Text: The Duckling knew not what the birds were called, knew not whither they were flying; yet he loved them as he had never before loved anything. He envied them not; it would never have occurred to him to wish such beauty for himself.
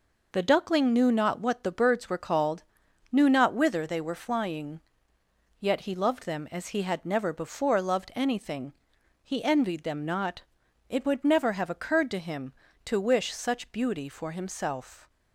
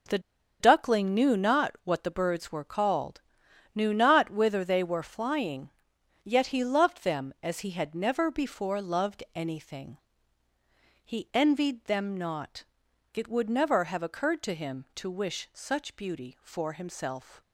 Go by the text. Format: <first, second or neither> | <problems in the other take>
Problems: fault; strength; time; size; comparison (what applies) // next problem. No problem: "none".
first | pauses between "The" and "Duckling"; at 0.1 s; 0.41 s long